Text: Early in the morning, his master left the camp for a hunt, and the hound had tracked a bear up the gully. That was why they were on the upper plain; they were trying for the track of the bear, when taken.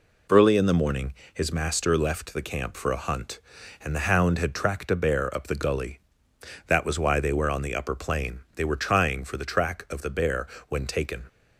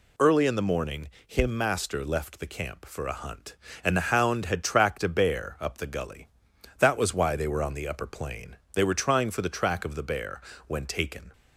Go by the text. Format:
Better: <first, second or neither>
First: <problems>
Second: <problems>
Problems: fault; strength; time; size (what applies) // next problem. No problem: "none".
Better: first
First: none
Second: says "him" for "his"; at 1.2 s